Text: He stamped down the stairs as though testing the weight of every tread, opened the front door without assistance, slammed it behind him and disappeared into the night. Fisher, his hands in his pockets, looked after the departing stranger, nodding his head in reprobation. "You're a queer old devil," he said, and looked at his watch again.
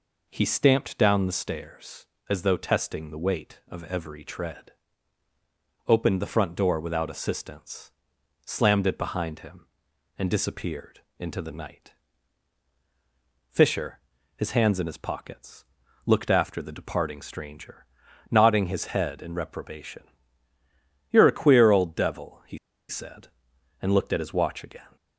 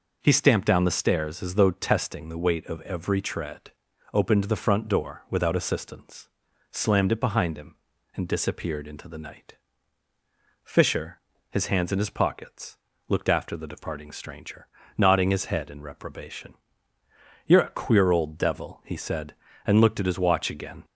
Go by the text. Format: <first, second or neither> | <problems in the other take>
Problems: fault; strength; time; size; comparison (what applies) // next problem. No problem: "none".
second | pauses between "disappeared" and "into"; slight; at 10.9 s; 0.18 s long // pauses between "he" and "said"; slight; at 22.5 s; 0.31 s long